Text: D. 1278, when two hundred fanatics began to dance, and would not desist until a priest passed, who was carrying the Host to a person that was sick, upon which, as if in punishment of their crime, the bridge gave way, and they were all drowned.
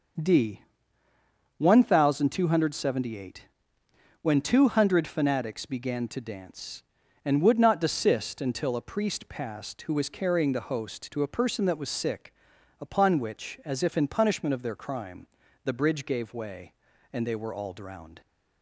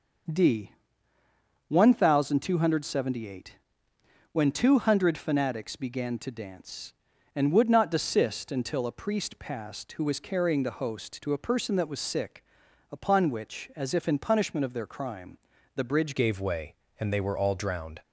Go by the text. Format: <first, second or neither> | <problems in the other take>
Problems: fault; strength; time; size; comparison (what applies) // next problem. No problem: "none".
first | starts louder than the rest; until 2.2 s; 6 dB; also in the first // changes voice at "gave"; from 16.1 s on; 1.9 s long